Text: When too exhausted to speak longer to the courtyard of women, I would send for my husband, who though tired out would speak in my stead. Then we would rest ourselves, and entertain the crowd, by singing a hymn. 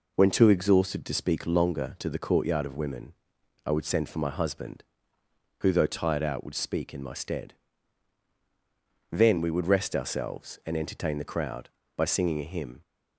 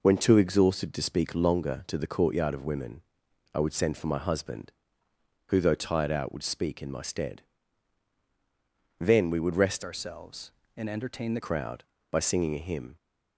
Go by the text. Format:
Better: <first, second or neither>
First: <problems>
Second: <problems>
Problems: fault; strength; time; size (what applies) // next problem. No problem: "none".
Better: first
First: none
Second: changes voice from "ourselves" to "the"; from 9.8 to 11.4 s; 1.6 s long